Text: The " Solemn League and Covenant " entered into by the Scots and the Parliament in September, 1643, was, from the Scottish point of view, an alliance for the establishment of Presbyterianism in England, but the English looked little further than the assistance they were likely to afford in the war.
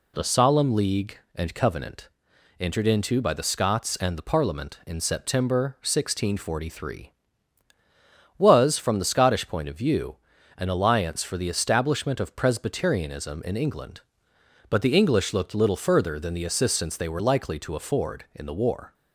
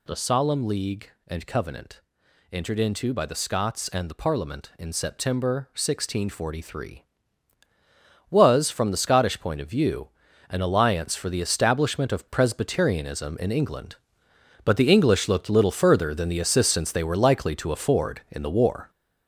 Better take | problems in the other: first | gets louder; strong; throughout; 8 dB

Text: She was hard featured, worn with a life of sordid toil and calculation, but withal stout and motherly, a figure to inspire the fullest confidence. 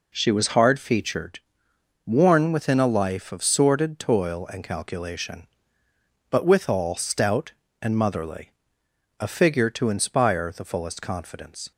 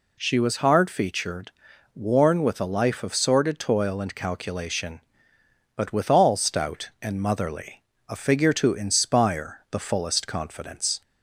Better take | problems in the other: second | says "within" for "with"; at 2.5 s

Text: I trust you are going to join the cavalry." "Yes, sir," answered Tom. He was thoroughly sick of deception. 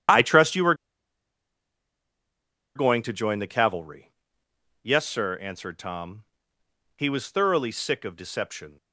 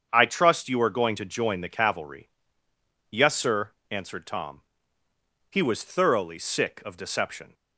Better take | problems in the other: second | starts louder than the rest; strong; until 3.1 s; 9 dB; strong in the second // pauses between "are" and "going"; strong; at 0.7 s; 2.0 s long

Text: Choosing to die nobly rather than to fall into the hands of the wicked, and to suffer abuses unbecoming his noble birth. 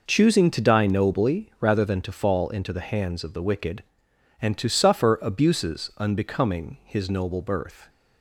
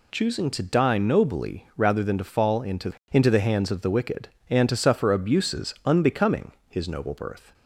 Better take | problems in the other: first | says "into" twice; at 3.1 s // pauses between "unbecoming" and "his"; slight; at 6.5 s; 0.18 s long

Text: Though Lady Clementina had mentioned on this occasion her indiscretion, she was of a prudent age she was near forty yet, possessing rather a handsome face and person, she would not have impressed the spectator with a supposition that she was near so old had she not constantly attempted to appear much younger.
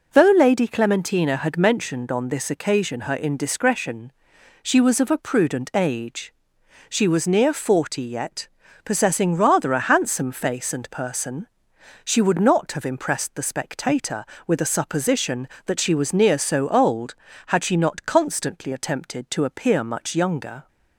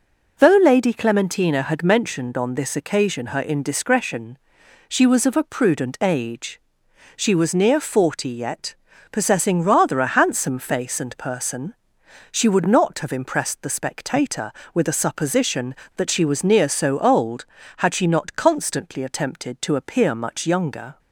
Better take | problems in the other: neither | pauses between "age" and "she"; noticeable; the same in both

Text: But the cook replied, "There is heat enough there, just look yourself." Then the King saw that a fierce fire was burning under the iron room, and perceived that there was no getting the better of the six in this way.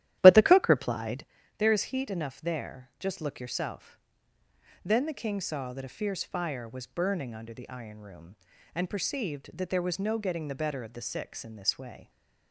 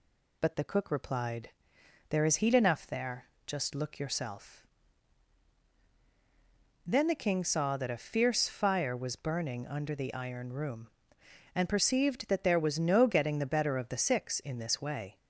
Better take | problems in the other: second | starts louder than the rest; strong; until 1.3 s; 13 dB

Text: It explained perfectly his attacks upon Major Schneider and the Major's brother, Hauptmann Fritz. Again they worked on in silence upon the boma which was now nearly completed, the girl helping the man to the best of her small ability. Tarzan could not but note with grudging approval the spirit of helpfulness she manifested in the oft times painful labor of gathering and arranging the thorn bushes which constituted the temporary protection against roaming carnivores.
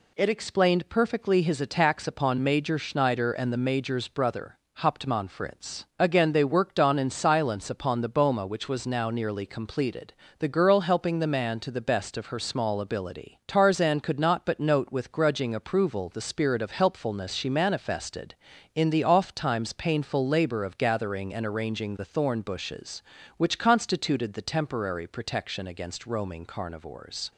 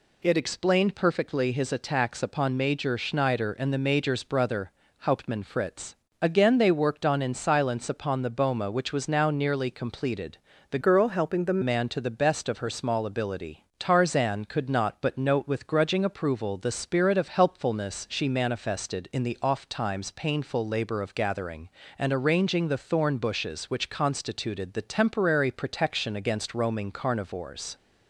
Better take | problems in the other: first | changes voice from "girl" to "the"; from 10.8 to 11.5 s; 0.7 s long

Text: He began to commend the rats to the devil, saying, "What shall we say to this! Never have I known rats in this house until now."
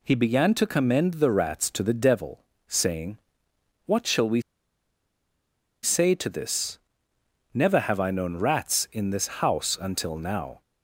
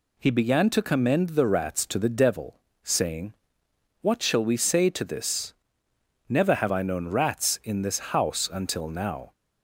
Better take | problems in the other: second | pauses between "we" and "say"; strong; at 4.4 s; 1.4 s long

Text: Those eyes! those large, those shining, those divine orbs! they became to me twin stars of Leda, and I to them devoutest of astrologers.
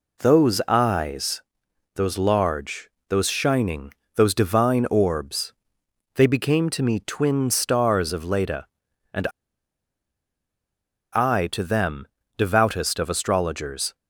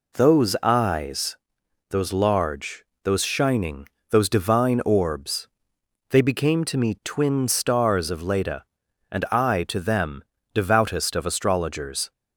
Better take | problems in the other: second | pauses between "and" and "I"; strong; at 9.2 s; 1.8 s long // pauses between "them" and "devoutest"; slight; at 12.0 s; 0.32 s long; slight in the second

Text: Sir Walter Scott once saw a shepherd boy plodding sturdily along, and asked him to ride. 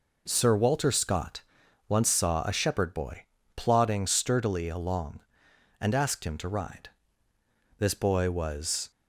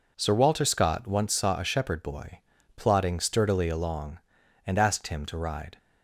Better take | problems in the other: second | pauses between "Scott" and "once"; at 1.4 s; 0.44 s long // pauses between "boy" and "plodding"; slight; at 3.2 s; 0.32 s long; also in the second // goes on to say "This boy was"; noticeable; from 7.7 s on; 1.1 s long

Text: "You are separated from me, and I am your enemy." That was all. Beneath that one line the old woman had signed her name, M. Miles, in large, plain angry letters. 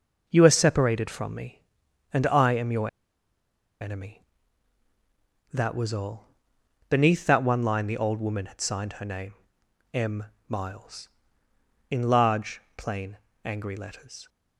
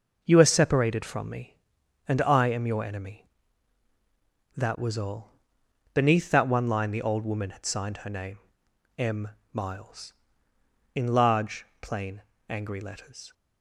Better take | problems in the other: second | pauses between "your" and "enemy"; noticeable; at 2.8 s; 0.91 s long // pauses between "plain" and "angry"; slight; at 13.1 s; 0.26 s long; slight in the second

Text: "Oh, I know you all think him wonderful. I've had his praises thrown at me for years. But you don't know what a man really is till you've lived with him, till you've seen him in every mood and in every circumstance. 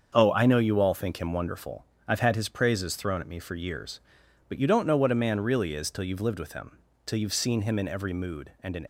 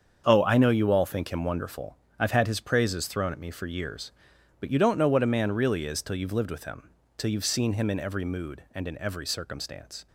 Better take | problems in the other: second | starts louder than the rest; until 1.1 s; 7 dB; strong in the second // stops before "every circumstance"; at 8.8 s

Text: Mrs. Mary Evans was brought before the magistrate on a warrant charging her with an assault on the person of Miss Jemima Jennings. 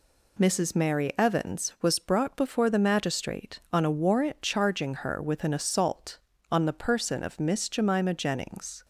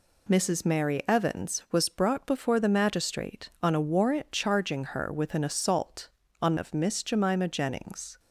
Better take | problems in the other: first | skips "the person"; at 6.5 s

